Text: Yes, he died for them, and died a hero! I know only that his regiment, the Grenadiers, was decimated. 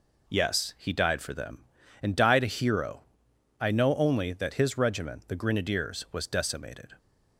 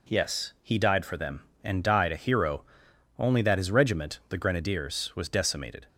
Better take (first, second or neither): first